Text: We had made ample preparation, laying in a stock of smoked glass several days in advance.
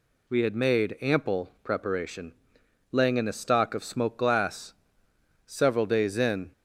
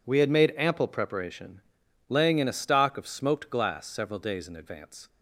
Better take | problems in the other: second | pauses between "glass" and "several"; noticeable; at 4.7 s; 0.72 s long // stops before "advance"; at 6.5 s

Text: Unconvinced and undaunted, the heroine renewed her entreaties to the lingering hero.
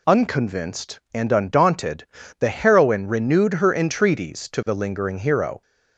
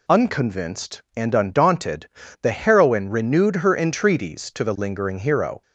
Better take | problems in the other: neither | none

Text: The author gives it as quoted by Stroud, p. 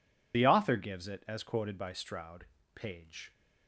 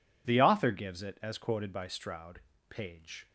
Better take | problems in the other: second | loses the start of "The"; at 0.3 s; 45 ms

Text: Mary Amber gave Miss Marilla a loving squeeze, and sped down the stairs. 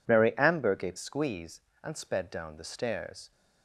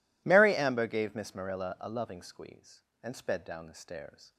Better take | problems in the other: second | skips "Miss Marilla a loving"; at 0.9 s

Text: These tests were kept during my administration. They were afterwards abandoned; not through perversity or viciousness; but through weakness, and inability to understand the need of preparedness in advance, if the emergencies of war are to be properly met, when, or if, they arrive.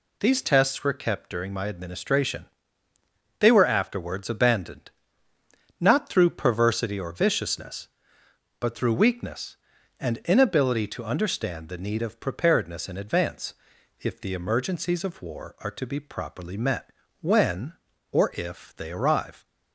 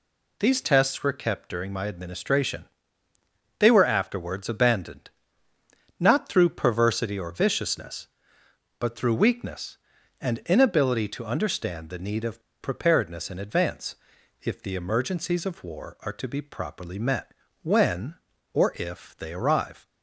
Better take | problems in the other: first | pauses between "of" and "preparedness"; slight; at 12.4 s; 0.20 s long

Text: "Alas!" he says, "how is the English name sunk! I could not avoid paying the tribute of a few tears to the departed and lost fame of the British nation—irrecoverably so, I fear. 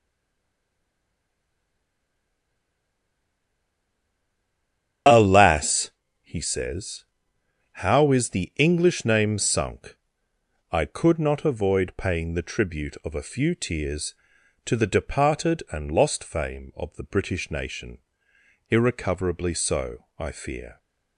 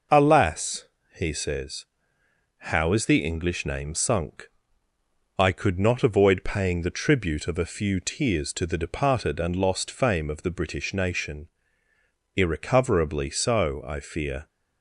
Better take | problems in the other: second | stays silent before the first word; strong; until 5.0 s; 5.0 s long // starts louder than the rest; strong; until 6.3 s; 9 dB

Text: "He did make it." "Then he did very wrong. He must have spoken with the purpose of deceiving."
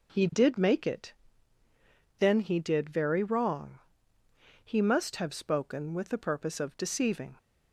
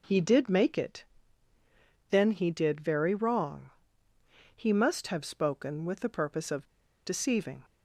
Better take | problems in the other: first | pauses between "of" and "deceiving"; at 6.6 s; 0.37 s long

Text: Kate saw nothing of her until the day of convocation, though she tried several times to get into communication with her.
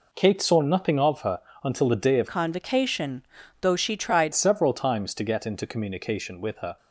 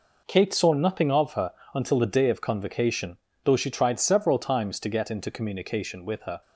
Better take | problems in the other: second | pauses between "her" and "until"; slight; at 1.3 s; 0.24 s long; slight in the second // changes voice from "convocation" to "tried"; from 2.2 to 4.3 s; 2.1 s long

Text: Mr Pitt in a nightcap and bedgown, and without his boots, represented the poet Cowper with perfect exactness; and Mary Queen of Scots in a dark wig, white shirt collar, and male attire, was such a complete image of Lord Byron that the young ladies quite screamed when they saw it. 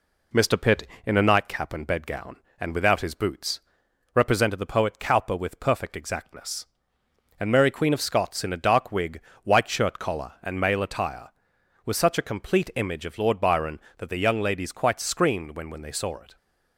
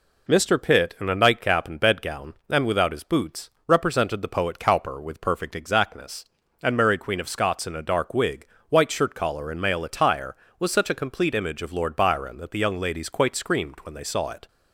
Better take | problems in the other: second | says "when" twice; at 15.6 s

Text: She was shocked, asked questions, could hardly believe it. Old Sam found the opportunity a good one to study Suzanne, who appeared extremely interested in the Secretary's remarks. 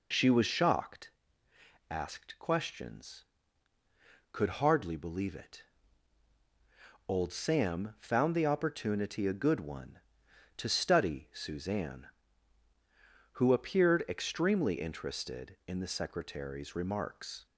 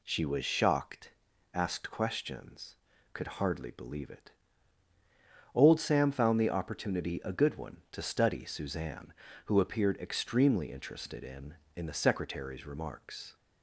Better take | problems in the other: first | says "in" twice; at 11.7 s

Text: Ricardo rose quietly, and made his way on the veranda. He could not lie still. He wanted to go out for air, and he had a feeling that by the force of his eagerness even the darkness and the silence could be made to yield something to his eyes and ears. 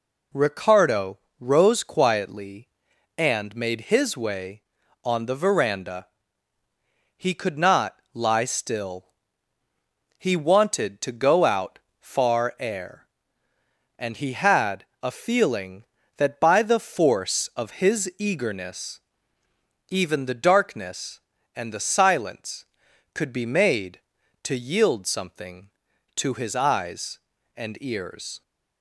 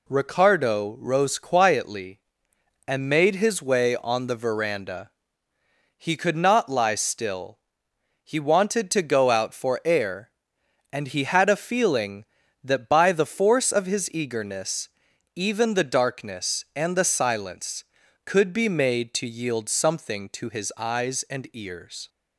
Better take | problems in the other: second | pauses between "Ricardo" and "rose"; slight; at 1.1 s; 0.24 s long // pauses between "not" and "lie"; slight; at 7.9 s; 0.18 s long // says "far" for "for"; at 11.9 s // pauses between "had" and "a"; slight; at 14.8 s; 0.18 s long // pauses between "eagerness" and "even"; noticeable; at 18.9 s; 0.90 s long; noticeable in the second

